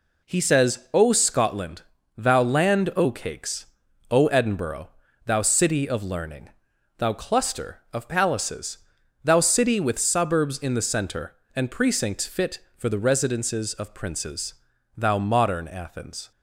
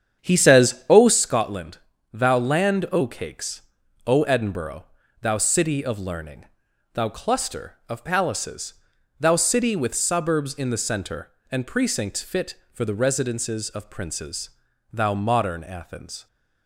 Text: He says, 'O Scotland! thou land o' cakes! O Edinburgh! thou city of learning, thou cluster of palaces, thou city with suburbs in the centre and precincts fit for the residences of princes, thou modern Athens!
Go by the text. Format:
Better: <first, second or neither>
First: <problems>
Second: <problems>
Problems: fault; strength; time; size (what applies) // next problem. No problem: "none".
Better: first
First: none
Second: starts louder than the rest; strong; until 1.2 s; 8 dB